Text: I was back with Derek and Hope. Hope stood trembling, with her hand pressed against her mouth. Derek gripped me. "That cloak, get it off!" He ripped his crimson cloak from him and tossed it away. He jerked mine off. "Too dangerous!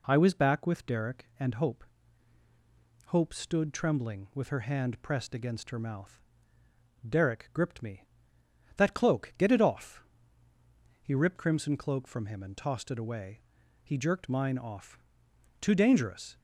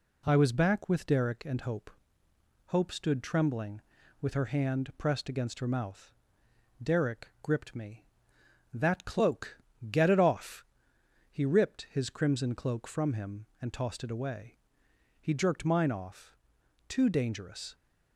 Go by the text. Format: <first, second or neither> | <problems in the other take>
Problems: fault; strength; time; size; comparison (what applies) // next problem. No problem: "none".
second | skips "his"; at 11.3 s